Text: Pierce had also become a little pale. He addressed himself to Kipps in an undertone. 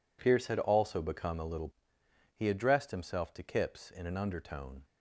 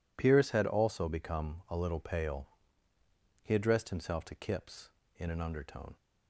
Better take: second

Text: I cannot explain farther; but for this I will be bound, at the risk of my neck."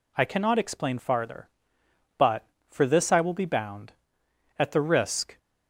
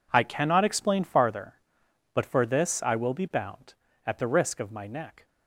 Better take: second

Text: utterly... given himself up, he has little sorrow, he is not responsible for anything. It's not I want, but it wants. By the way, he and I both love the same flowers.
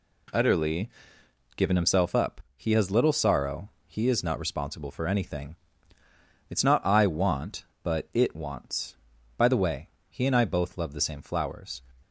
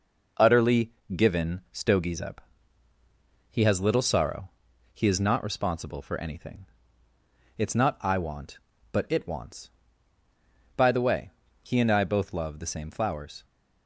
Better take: first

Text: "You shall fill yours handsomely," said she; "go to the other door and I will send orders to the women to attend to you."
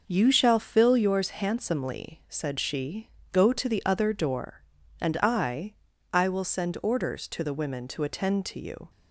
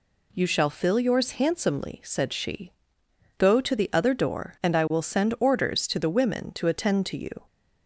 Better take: second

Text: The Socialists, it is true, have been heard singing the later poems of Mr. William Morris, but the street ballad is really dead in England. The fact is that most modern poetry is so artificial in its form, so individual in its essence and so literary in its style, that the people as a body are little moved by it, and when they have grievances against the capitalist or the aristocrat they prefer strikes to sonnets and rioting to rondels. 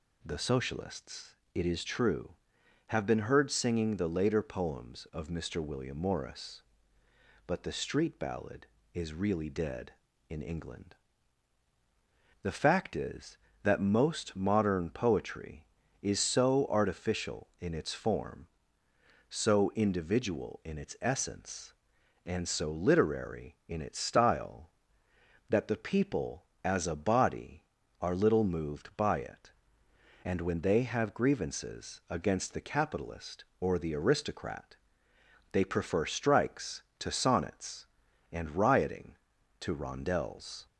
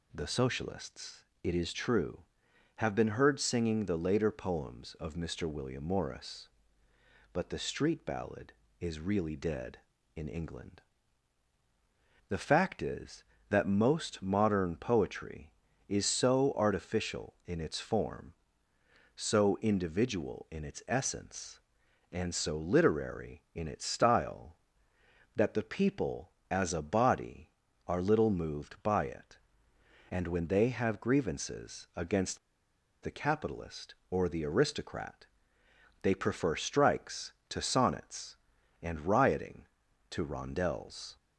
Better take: first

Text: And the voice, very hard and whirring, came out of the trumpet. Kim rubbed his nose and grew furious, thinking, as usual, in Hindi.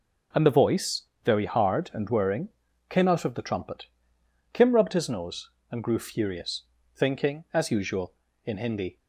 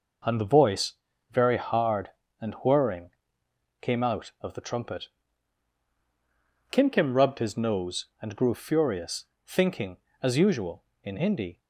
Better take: first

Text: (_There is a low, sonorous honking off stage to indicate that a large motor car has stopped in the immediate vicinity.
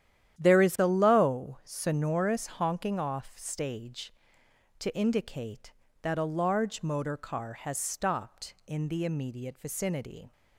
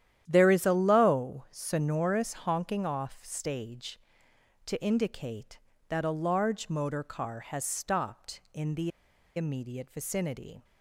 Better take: first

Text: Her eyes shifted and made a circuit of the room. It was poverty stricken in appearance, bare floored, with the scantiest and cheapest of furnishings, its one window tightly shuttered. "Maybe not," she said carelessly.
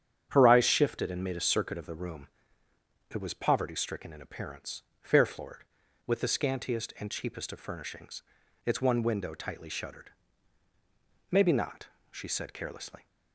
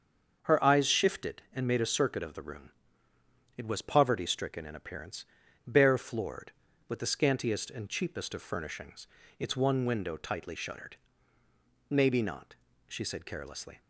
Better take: second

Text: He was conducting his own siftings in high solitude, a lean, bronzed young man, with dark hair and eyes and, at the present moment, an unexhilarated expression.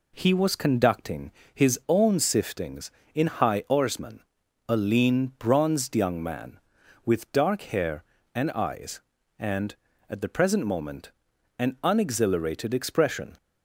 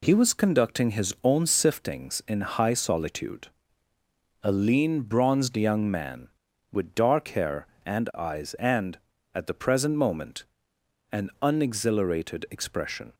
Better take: second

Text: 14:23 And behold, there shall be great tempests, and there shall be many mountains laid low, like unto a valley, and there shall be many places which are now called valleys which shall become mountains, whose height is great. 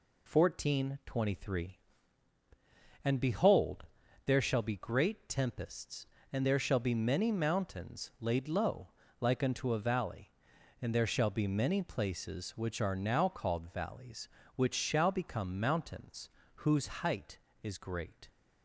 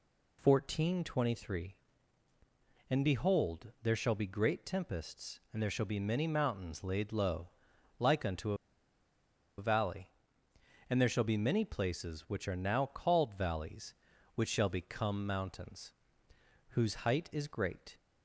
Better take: first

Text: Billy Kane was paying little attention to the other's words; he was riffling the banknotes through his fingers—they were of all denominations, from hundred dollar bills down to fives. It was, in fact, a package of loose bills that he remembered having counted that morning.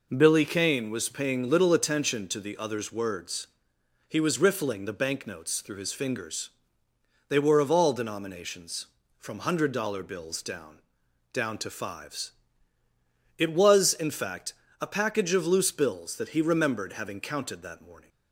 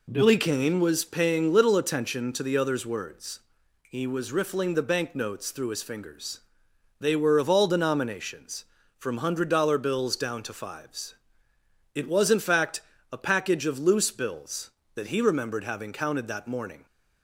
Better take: second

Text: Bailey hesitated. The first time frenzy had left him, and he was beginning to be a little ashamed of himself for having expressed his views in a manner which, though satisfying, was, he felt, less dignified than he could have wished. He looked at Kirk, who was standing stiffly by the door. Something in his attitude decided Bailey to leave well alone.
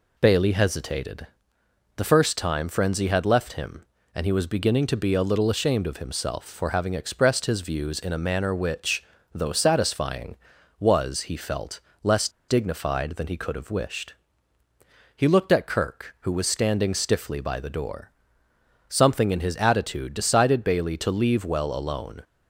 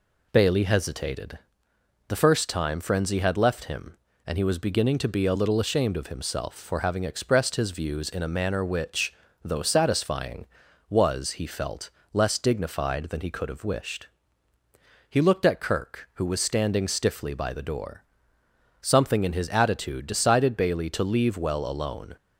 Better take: second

